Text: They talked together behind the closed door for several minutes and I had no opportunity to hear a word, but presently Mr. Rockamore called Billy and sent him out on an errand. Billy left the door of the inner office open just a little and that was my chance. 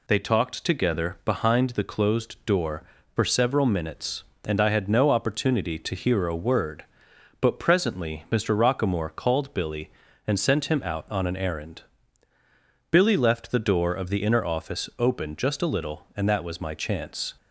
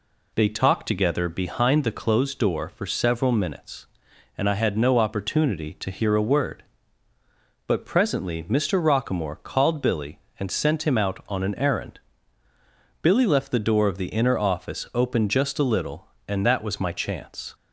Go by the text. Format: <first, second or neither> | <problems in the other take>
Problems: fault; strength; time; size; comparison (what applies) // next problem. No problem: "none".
neither | none